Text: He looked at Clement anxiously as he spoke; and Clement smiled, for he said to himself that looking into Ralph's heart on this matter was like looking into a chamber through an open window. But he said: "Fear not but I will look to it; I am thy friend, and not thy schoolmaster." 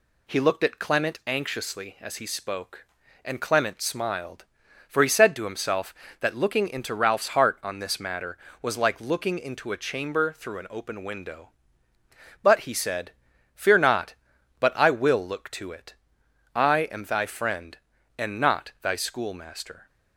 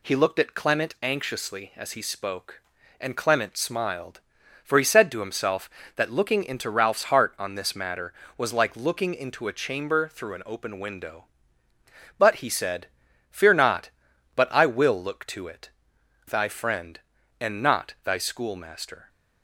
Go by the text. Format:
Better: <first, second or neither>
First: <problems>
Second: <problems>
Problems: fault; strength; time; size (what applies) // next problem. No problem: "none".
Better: first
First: none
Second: skips "I am"; at 15.9 s